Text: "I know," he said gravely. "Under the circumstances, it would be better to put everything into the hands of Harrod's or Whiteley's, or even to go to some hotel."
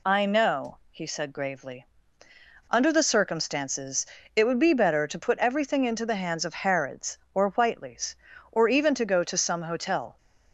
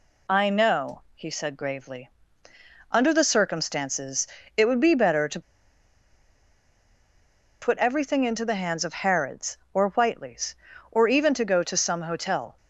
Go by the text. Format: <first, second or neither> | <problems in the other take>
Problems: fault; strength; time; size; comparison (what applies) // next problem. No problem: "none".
first | pauses between "to" and "put"; strong; at 5.4 s; 2.2 s long